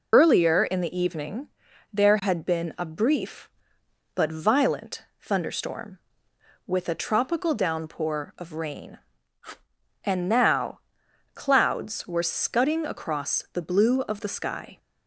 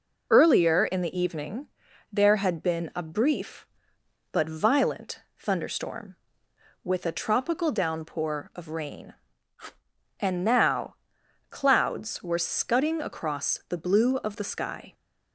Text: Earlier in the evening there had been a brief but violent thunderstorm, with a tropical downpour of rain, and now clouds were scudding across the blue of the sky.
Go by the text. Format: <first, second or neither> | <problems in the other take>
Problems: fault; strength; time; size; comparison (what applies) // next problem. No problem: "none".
second | loses the start of "Earlier"; at 0.1 s; 30 ms // pauses between "evening" and "there"; at 1.4 s; 0.44 s long; also in the second // pauses between "violent" and "thunderstorm"; slight; at 5.0 s; 0.16 s long; slight in the second // pauses between "now" and "clouds"; noticeable; at 10.8 s; 0.54 s long; noticeable in the second